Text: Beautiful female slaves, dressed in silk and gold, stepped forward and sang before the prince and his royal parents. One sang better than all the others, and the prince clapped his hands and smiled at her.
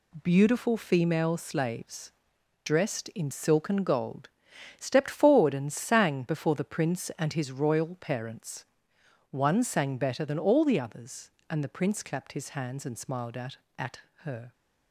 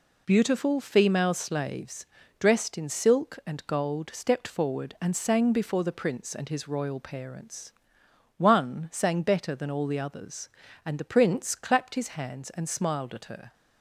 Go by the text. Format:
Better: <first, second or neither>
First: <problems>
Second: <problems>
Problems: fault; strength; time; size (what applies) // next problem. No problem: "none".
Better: second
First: says "at" twice; at 13.7 s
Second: none